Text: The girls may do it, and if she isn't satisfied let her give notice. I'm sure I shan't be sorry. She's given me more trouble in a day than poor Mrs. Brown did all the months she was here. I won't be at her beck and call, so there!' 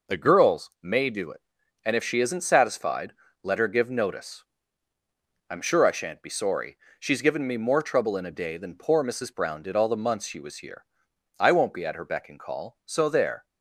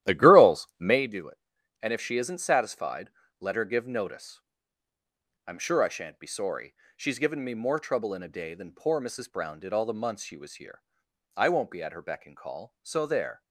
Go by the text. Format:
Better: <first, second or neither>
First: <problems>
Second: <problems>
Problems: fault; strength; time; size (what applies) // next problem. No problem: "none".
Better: first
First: pauses between "satisfied" and "let"; slight; at 3.1 s; 0.32 s long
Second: starts louder than the rest; strong; until 1.0 s; 13 dB // pauses between "satisfied" and "let"; slight; at 3.0 s; 0.32 s long